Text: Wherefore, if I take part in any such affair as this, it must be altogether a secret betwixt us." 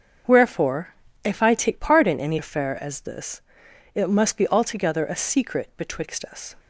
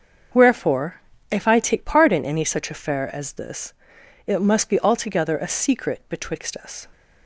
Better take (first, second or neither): second